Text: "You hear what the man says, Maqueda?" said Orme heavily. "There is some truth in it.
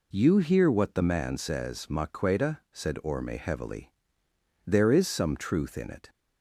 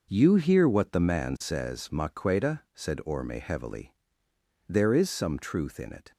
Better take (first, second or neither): first